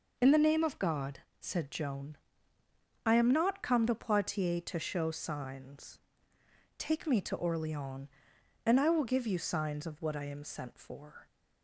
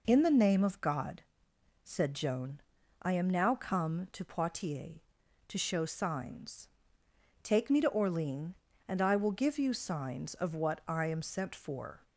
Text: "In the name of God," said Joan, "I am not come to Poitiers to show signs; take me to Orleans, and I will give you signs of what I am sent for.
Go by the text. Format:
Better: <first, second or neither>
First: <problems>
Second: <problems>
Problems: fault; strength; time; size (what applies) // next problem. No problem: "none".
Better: first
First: none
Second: says "now" for "not"; at 3.2 s